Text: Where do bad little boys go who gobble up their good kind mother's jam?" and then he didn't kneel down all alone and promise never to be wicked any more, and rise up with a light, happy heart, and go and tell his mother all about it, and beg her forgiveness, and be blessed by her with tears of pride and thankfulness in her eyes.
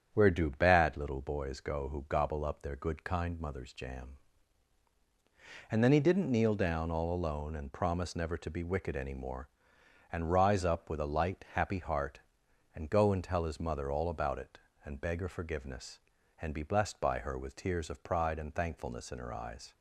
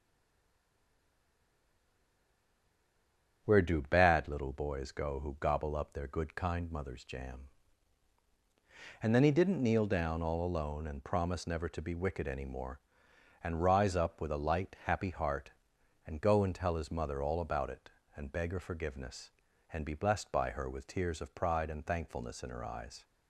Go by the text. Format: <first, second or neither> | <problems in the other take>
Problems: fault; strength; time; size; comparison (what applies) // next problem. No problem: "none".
first | stays silent before the first word; strong; until 3.4 s; 3.4 s long // starts louder than the rest; strong; until 4.4 s; 8 dB; strong in the first